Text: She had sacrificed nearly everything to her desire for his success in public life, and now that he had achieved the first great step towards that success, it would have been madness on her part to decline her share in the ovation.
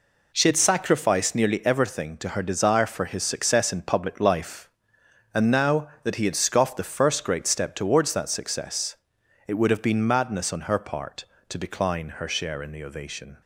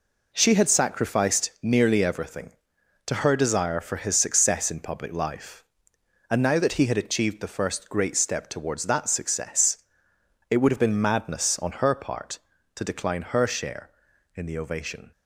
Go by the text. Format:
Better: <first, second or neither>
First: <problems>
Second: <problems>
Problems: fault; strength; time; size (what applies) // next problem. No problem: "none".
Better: second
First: says "scoffed" for "achieved"; at 6.3 s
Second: none